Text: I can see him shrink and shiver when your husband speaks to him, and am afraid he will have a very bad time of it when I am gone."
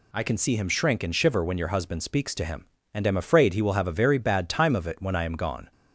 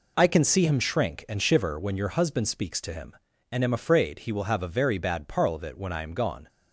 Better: first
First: none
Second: says "parl" for "time"; at 5.2 s

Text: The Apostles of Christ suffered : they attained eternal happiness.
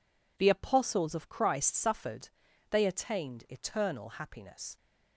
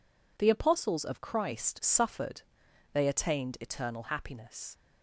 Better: neither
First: none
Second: none

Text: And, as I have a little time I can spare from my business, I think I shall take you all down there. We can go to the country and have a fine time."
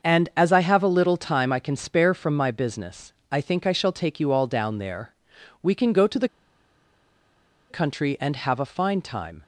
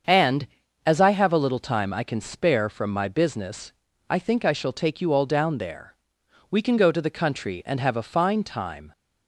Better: second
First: starts louder than the rest; until 1.1 s; 6.5 dB // pauses between "the" and "country"; strong; at 6.2 s; 1.4 s long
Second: starts louder than the rest; until 1.4 s; 7 dB

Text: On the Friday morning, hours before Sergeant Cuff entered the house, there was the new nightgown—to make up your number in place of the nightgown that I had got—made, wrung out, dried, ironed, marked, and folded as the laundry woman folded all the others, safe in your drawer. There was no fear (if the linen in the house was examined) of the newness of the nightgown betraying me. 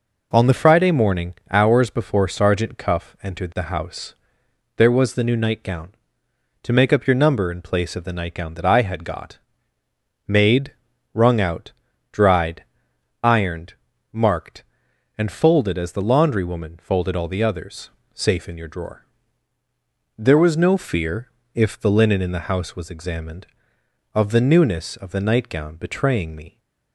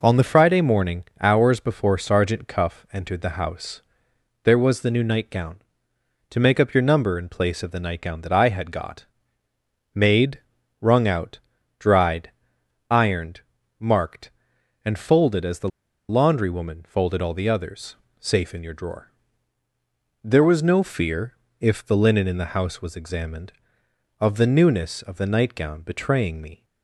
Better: first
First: none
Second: pauses between "the" and "laundry"; at 15.6 s; 0.41 s long

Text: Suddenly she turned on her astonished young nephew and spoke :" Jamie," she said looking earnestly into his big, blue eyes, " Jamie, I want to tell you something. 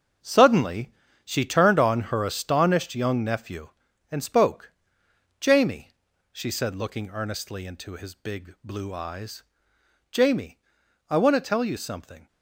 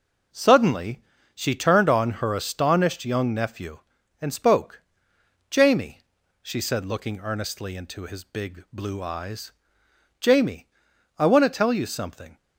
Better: second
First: gets quieter; strong; throughout; 12.5 dB // starts louder than the rest; strong; until 1.5 s; 8 dB // pauses between "Suddenly" and "she"; slight; at 0.9 s; 0.32 s long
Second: starts louder than the rest; until 1.6 s; 6.5 dB // pauses between "Suddenly" and "she"; slight; at 1.0 s; 0.32 s long

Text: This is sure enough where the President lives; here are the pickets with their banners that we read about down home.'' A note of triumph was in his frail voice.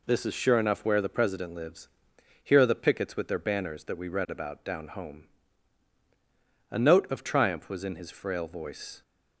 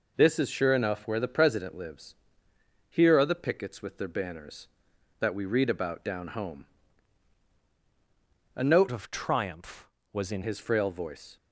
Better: first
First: none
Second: changes voice from "of" to "in"; from 8.8 to 10.4 s; 1.6 s long

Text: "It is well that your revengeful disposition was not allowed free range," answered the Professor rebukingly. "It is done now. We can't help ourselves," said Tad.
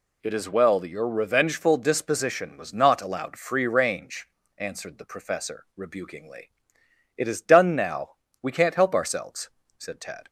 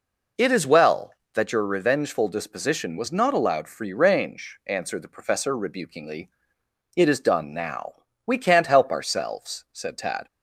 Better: neither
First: none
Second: none

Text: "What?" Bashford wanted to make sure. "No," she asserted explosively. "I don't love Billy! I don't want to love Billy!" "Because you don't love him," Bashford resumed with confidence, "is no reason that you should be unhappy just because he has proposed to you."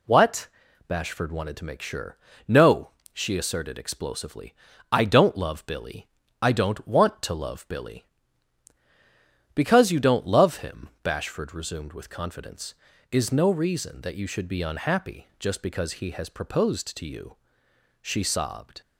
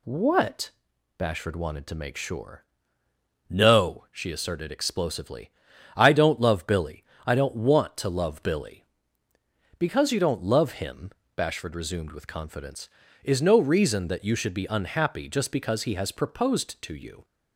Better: second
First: goes on to say "She sobbed"; noticeable; from 18.0 s on; 0.80 s long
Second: none

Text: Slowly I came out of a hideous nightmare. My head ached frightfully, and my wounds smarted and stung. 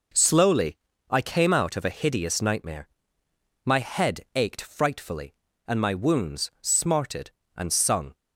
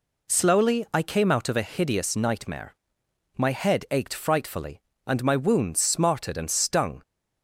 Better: second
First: pauses between "Slowly" and "I"; slight; at 0.7 s; 0.32 s long // says "sung" for "stung"; at 7.7 s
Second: none

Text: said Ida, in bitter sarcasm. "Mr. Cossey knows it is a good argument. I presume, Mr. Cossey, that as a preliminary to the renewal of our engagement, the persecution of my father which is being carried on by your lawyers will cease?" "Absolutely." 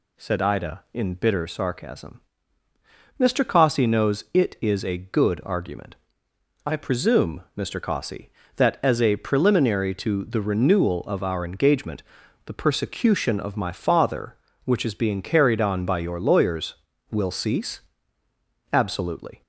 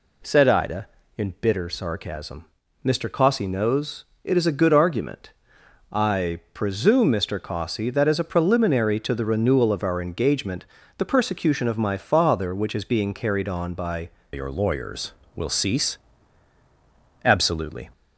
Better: first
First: none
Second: pauses between "knows" and "it"; slight; at 4.0 s; 0.18 s long // changes voice at "your"; from 14.3 s on; 3.5 s long

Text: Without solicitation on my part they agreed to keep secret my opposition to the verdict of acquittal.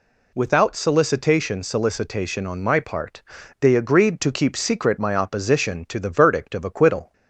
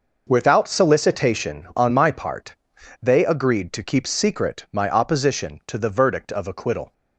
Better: second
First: says "solicitation" twice; at 1.6 s // pauses between "part" and "they"; at 3.2 s; 0.40 s long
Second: pauses between "part" and "they"; at 2.5 s; 0.44 s long

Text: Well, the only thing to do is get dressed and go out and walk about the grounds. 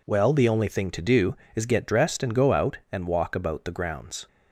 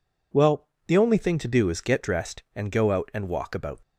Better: first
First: none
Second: stops before "the grounds"; at 3.8 s

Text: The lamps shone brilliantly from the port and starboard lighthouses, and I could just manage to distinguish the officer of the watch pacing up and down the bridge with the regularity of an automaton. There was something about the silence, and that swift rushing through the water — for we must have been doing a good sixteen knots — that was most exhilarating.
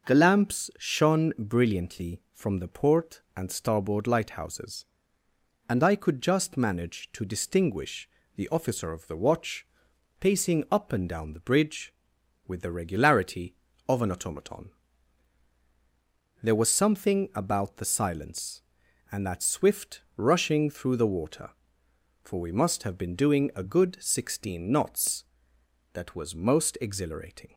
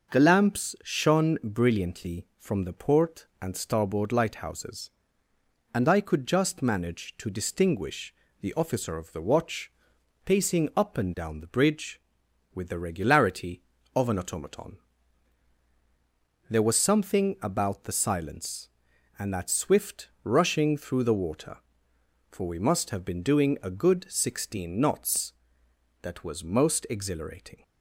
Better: neither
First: starts louder than the rest; noticeable; until 1.1 s; 6 dB // pauses between "distinguish" and "the"; slight; at 8.0 s; 0.26 s long // pauses between "watch" and "pacing"; noticeable; at 9.6 s; 0.54 s long // pauses between "swift" and "rushing"; slight; at 20.0 s; 0.16 s long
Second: starts louder than the rest; noticeable; until 1.1 s; 6 dB // pauses between "distinguish" and "the"; slight; at 8.1 s; 0.26 s long // pauses between "watch" and "pacing"; noticeable; at 9.7 s; 0.54 s long // pauses between "swift" and "rushing"; slight; at 20.0 s; 0.16 s long

